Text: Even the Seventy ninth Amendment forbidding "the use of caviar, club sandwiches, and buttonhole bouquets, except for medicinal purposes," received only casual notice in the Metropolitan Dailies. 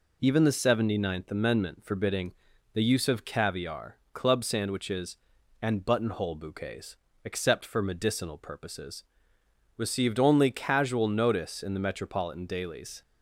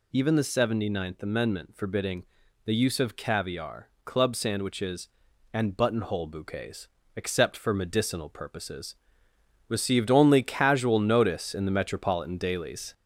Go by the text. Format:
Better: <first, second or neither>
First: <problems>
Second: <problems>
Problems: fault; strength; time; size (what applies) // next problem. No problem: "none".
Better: first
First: pauses between "forbidding" and "the"; at 2.3 s; 0.40 s long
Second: gets louder; slight; throughout; 3.5 dB // pauses between "forbidding" and "the"; at 2.2 s; 0.40 s long